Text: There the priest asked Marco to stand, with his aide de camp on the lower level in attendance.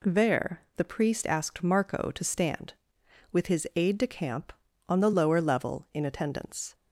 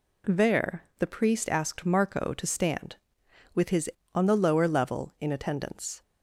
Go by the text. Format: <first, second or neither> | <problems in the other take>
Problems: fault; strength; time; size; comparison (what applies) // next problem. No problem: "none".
first | skips "aide de camp"; at 4.0 s